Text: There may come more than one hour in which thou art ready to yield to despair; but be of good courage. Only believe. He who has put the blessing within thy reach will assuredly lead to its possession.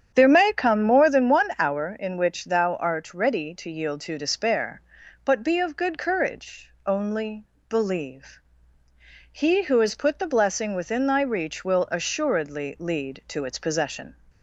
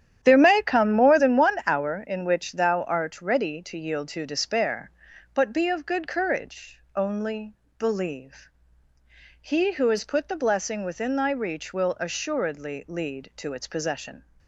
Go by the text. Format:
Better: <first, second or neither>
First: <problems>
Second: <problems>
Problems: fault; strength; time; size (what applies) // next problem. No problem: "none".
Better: first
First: starts louder than the rest; strong; until 1.1 s; 8.5 dB // pauses between "Only" and "believe"; slight; at 7.4 s; 0.24 s long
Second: gets quieter; strong; throughout; 10.5 dB // starts louder than the rest; strong; until 1.2 s; 10.5 dB // pauses between "Only" and "believe"; slight; at 7.5 s; 0.24 s long